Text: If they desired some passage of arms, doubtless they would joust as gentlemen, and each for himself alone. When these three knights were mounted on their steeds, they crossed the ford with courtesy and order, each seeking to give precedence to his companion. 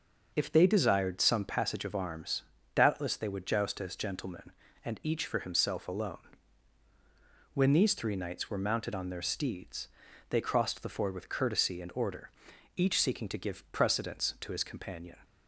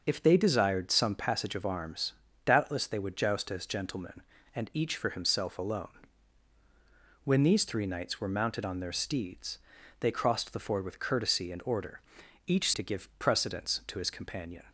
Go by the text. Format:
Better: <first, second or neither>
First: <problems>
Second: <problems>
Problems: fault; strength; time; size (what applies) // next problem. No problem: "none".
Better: first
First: none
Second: skips "seeking"; at 12.7 s